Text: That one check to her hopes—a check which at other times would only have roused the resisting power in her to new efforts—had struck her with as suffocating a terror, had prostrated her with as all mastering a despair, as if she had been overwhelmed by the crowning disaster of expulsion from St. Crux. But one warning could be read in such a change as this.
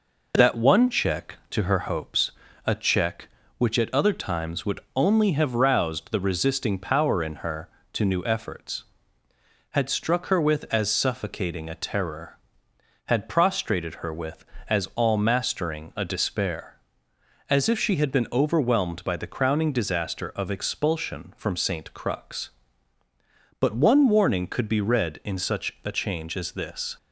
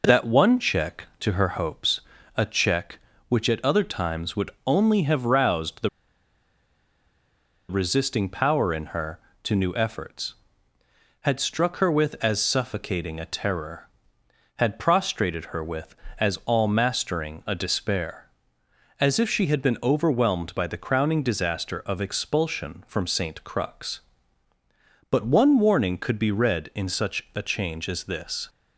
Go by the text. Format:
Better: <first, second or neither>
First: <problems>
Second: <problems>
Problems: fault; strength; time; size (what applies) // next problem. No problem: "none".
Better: first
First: pauses between "would" and "only"; slight; at 4.8 s; 0.16 s long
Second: pauses between "would" and "only"; slight; at 4.5 s; 0.16 s long // pauses between "the" and "resisting"; strong; at 5.8 s; 1.7 s long